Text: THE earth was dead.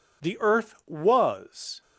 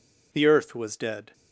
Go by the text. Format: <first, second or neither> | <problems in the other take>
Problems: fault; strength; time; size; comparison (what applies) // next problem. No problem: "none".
second | stops before "dead"; at 1.8 s